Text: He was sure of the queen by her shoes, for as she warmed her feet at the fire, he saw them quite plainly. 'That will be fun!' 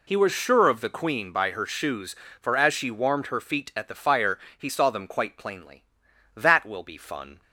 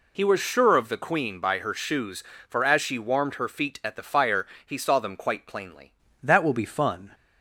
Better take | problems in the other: first | changes voice at "That"; from 6.2 s on; 0.9 s long

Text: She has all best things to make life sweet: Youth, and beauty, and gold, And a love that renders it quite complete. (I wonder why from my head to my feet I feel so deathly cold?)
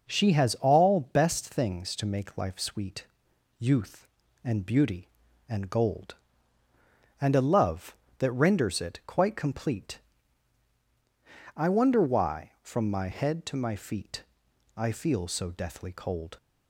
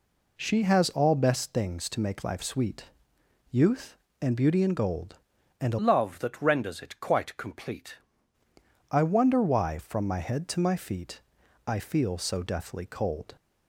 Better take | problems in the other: first | changes voice from "love" to "complete"; from 5.7 to 7.9 s; 2.2 s long // pauses between "feet" and "I"; at 11.2 s; 0.44 s long; noticeable in the first

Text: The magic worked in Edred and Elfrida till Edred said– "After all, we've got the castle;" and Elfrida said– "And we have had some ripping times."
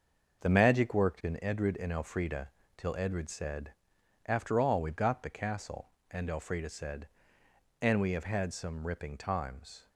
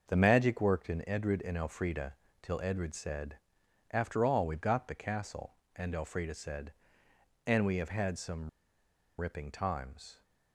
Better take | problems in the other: first | starts louder than the rest; until 1.0 s; 6 dB; also in the first // pauses between "Elfrida" and "till"; slight; at 2.1 s; 0.28 s long; slight in the first // pauses between "some" and "ripping"; noticeable; at 8.4 s; 0.71 s long

